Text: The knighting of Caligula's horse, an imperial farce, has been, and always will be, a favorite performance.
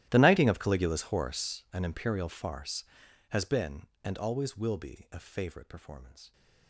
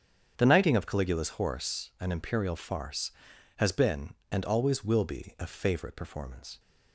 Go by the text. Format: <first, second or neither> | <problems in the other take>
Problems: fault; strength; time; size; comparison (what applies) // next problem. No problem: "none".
second | gets quieter; strong; throughout; 22 dB // starts louder than the rest; strong; until 1.1 s; 14 dB; strong in the second